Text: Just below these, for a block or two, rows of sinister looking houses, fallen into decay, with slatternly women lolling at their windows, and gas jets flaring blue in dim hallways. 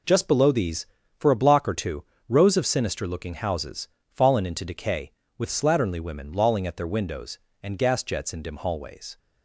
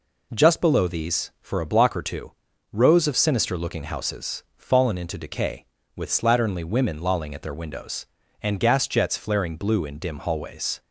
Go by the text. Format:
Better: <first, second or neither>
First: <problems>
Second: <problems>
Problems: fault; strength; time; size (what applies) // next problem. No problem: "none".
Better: second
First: skips "flaring blue"; at 8.3 s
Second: none